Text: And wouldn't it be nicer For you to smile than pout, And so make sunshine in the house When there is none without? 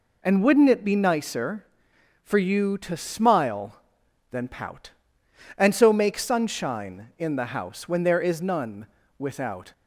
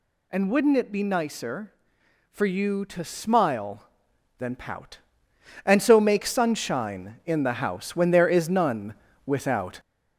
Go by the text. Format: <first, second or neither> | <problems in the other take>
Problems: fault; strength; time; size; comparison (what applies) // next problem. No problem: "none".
first | gets louder; throughout; 3.5 dB // pauses between "none" and "without"; slight; at 8.9 s; 0.32 s long; slight in the first